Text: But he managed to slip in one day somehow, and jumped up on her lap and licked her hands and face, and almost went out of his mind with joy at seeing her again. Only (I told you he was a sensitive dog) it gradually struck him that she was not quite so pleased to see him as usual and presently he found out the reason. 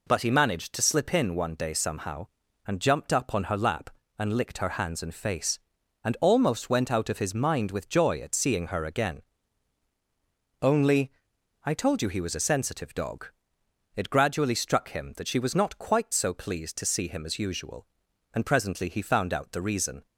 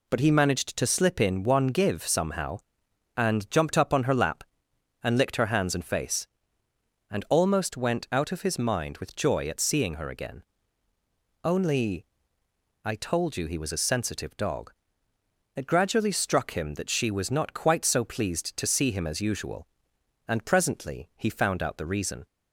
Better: first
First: none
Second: says "give" for "day"; at 1.6 s

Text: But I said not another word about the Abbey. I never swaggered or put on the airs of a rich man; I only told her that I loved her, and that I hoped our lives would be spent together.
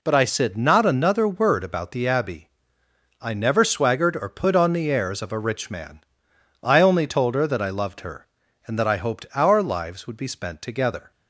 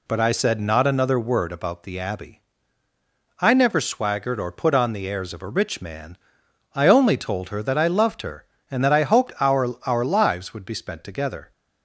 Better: first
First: none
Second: says "our" twice; at 9.8 s

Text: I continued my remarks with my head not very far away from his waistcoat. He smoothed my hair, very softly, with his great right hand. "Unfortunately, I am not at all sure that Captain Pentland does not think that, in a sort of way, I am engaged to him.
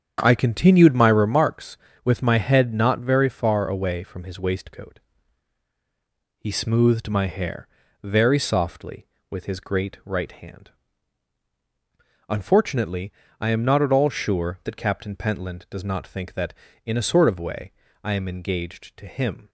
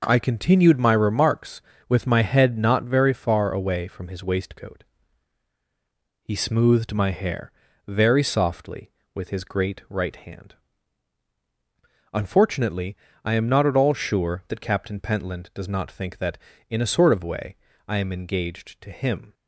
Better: second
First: starts louder than the rest; strong; until 1.4 s; 8 dB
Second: none

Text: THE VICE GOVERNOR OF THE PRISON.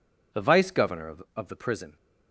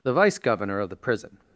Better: second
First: says "OF" twice; at 1.3 s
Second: none

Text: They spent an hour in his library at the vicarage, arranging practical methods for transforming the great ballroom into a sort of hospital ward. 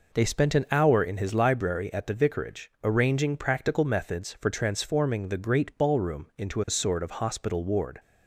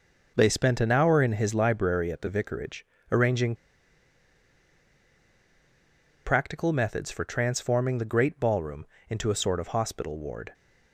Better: first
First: none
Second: pauses between "arranging" and "practical"; strong; at 3.5 s; 2.7 s long // pauses between "ballroom" and "into"; slight; at 8.8 s; 0.22 s long

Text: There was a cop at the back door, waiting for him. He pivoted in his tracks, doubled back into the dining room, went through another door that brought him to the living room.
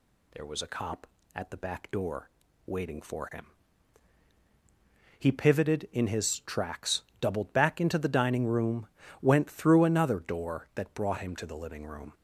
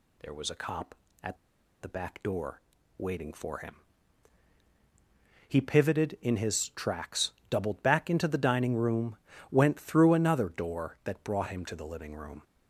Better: first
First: none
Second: pauses between "at" and "the"; at 1.3 s; 0.44 s long

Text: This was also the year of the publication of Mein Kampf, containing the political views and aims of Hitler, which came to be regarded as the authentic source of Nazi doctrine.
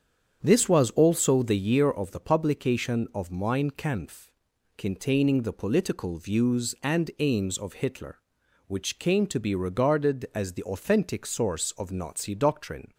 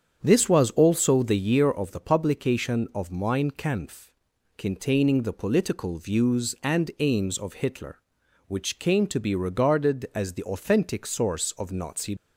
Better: first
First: starts louder than the rest; strong; until 1.4 s; 8 dB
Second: starts louder than the rest; strong; until 1.2 s; 8 dB // stops before "doctrine"; at 12.1 s

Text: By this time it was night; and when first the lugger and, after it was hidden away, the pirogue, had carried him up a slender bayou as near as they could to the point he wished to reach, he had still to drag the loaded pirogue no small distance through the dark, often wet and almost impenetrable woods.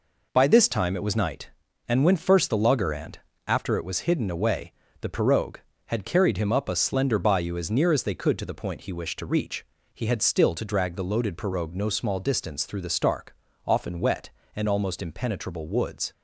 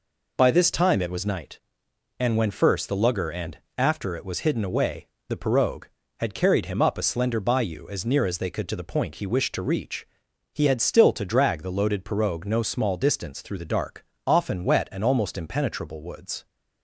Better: second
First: says "stark" for "dark"; at 12.8 s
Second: none

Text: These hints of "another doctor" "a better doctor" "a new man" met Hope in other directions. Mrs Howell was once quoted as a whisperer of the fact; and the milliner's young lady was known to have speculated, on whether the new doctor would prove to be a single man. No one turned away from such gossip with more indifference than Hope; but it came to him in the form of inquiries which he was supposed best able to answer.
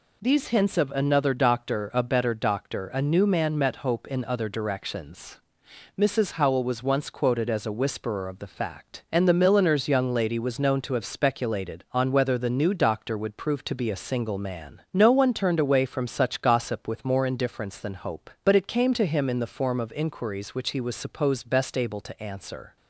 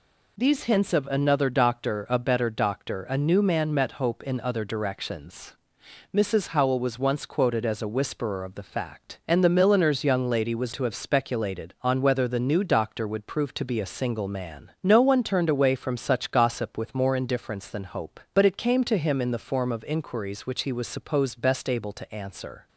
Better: first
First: none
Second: skips "known"; at 10.7 s

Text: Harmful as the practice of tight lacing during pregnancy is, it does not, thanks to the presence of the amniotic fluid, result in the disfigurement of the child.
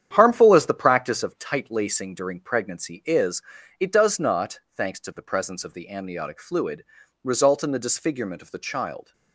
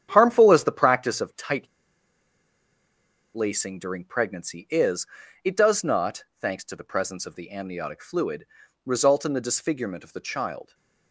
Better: first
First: starts louder than the rest; strong; until 1.1 s; 9.5 dB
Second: starts louder than the rest; strong; until 1.1 s; 9.5 dB // pauses between "tight" and "lacing"; strong; at 1.6 s; 1.6 s long

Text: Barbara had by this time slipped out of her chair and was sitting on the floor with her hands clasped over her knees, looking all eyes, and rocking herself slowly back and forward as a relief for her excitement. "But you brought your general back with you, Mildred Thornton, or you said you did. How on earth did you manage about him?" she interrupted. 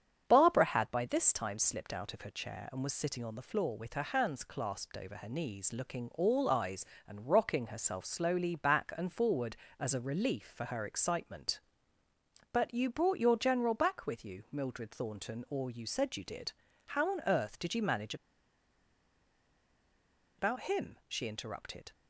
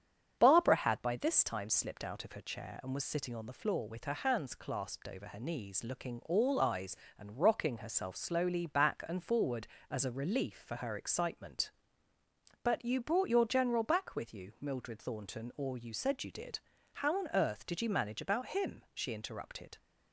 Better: second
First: starts louder than the rest; strong; until 1.2 s; 8.5 dB // pauses between "manage" and "about"; strong; at 18.1 s; 2.2 s long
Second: starts louder than the rest; strong; until 1.4 s; 8.5 dB

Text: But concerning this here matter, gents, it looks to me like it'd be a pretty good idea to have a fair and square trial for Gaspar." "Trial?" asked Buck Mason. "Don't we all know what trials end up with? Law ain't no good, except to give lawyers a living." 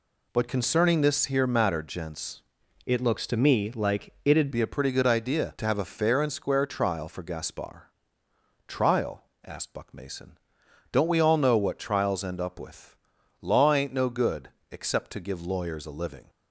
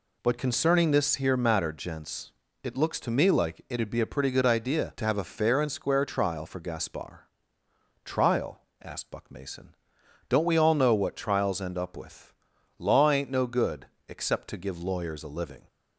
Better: second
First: changes voice from "it" to "it'd"; from 2.8 to 4.4 s; 1.6 s long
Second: none

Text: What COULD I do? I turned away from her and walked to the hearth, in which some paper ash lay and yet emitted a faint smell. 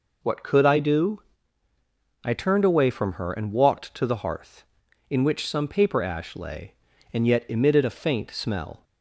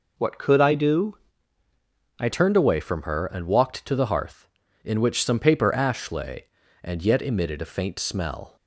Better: first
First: none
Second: changes voice at "turned"; from 2.3 s on; 6.2 s long

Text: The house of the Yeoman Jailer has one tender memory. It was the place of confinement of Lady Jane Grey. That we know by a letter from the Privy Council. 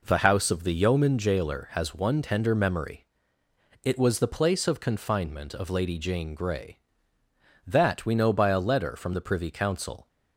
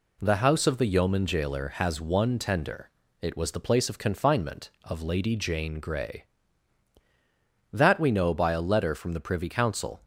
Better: first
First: none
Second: skips "memory"; at 3.0 s

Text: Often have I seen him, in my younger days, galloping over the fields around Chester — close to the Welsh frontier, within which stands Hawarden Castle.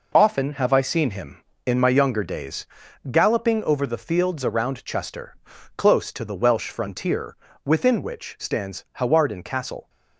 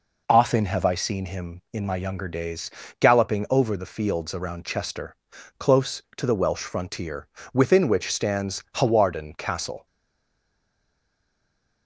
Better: first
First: none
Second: stays silent after the last word; noticeable; from 9.8 s on; 2.0 s long

